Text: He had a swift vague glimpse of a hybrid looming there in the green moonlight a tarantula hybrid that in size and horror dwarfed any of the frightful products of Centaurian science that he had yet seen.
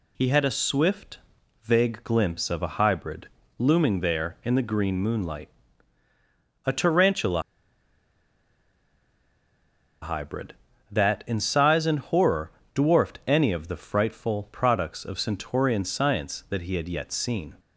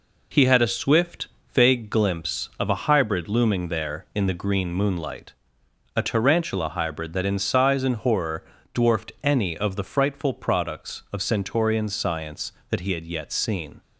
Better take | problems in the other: second | pauses between "swift" and "vague"; noticeable; at 1.1 s; 0.46 s long; slight in the second // pauses between "hybrid" and "looming"; slight; at 3.2 s; 0.30 s long // pauses between "moonlight" and "a"; at 5.5 s; 1.1 s long; noticeable in the second // pauses between "tarantula" and "hybrid"; strong; at 7.4 s; 2.5 s long // pauses between "horror" and "dwarfed"; slight; at 12.5 s; 0.22 s long; slight in the second

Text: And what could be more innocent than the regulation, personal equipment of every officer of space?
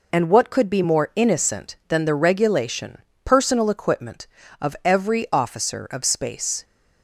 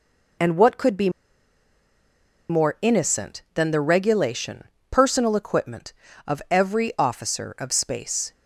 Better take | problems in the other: first | pauses between "be" and "more"; strong; at 1.0 s; 1.3 s long

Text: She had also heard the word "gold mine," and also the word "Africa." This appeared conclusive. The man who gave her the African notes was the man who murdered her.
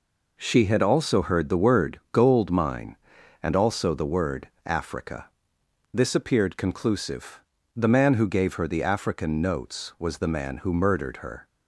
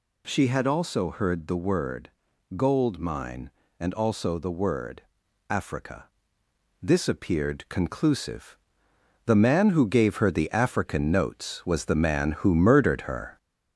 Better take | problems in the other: first | gets louder; slight; throughout; 2.5 dB // pauses between "word" and "gold"; noticeable; at 2.0 s; 0.46 s long // pauses between "word" and "Africa"; noticeable; at 5.0 s; 0.48 s long; slight in the first

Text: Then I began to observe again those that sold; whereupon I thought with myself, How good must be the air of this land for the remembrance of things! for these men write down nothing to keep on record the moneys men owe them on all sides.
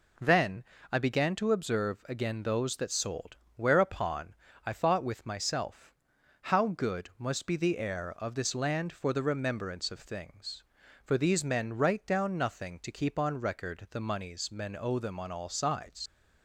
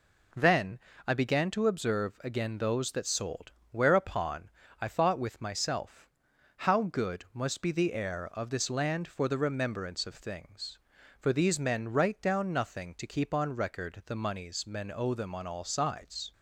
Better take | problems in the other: second | pauses between "Then" and "I"; slight; at 0.6 s; 0.28 s long; slight in the second // pauses between "whereupon" and "I"; slight; at 4.3 s; 0.32 s long; slight in the second // leaves "sides" unfinished; at 16.0 s; 110 ms

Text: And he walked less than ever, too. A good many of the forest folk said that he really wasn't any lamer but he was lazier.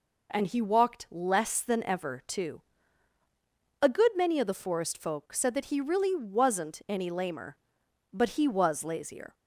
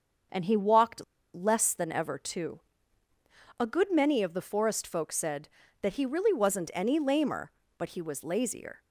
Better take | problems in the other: first | starts louder than the rest; until 1.6 s; 6.5 dB // pauses between "walked" and "less"; slight; at 1.0 s; 0.30 s long

